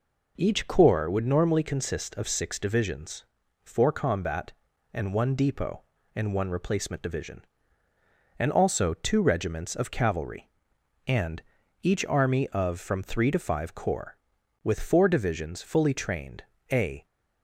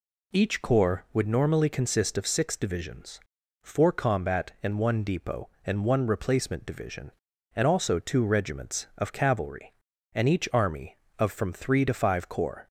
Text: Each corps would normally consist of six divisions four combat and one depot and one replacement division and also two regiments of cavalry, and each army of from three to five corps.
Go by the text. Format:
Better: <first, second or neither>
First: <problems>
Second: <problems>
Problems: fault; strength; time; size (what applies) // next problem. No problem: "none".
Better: second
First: pauses between "divisions" and "four"; at 3.2 s; 0.40 s long // pauses between "and" and "each"; at 11.4 s; 0.42 s long // goes on to say "With four divisions fully trained a"; strong; from 14.6 s on; 2.4 s long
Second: pauses between "divisions" and "four"; at 3.2 s; 0.42 s long